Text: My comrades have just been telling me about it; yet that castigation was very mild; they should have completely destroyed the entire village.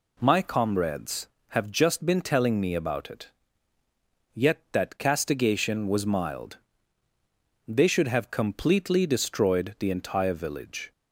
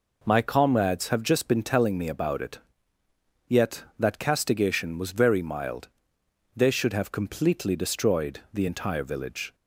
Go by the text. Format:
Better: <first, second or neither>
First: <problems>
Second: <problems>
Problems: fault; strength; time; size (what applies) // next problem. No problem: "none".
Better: second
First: skips "very"; at 6.0 s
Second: none